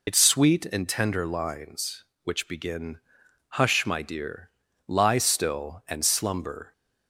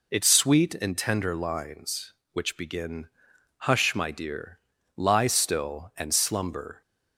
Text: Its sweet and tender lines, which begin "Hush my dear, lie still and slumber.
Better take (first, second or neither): second